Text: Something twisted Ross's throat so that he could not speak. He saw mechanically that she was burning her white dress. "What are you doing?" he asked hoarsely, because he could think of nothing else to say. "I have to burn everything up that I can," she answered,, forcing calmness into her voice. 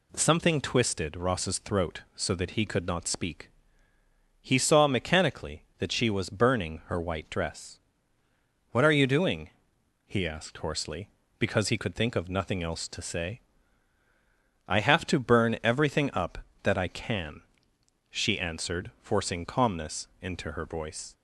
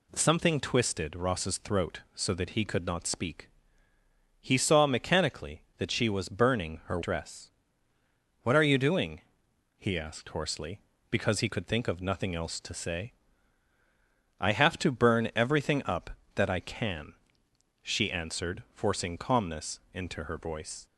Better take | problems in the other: first | skips "white"; at 7.0 s

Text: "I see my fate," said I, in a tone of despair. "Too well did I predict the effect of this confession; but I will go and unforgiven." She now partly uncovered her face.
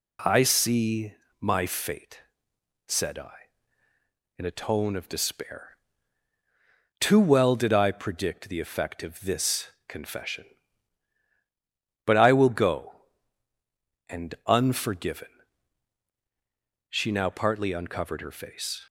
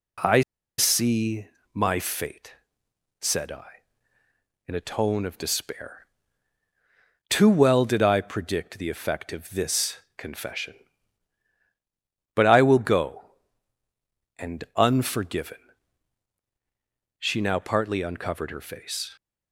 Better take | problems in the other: first | pauses between "I" and "see"; at 0.4 s; 0.37 s long // pauses between "see" and "my"; slight; at 1.4 s; 0.26 s long; slight in the first // pauses between "this" and "confession"; slight; at 9.9 s; 0.18 s long; slight in the first

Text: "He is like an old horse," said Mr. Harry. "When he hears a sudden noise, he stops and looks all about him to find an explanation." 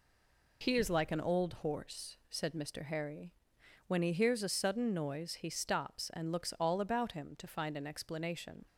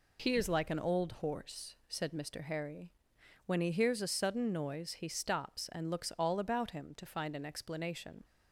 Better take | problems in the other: second | stays silent before the first word; slight; until 0.6 s; 0.6 s long

